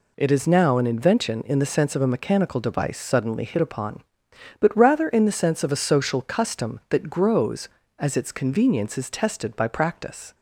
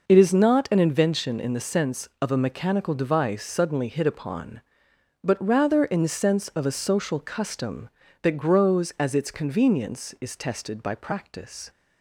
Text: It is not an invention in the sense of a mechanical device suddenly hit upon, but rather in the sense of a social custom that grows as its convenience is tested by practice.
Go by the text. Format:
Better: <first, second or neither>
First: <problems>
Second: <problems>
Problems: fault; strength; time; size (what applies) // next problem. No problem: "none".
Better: second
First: says "now" for "not"; at 0.4 s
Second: none